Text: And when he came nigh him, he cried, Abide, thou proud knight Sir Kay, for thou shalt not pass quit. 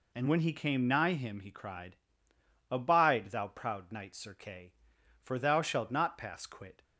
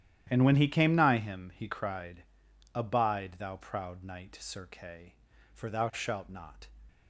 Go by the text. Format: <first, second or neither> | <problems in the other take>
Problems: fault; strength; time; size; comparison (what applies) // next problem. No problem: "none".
first | starts louder than the rest; strong; until 1.3 s; 11.5 dB // stops before "pass quit"; at 6.8 s